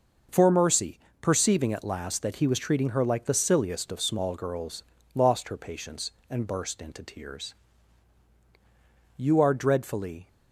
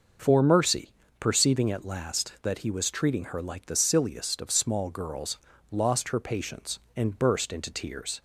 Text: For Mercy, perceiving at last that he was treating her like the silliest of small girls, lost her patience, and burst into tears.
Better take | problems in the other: second | goes on to say "You are dreadfully"; noticeable; from 9.1 s on; 1.1 s long

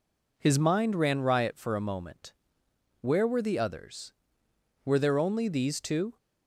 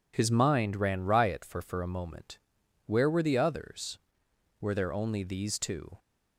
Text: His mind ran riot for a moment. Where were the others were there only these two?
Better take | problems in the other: first | says "for" twice; at 1.6 s

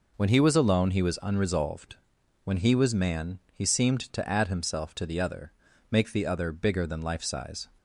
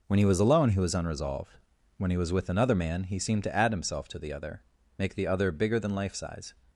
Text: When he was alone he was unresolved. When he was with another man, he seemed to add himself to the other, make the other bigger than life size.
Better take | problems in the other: second | skips "with another"; at 2.9 s

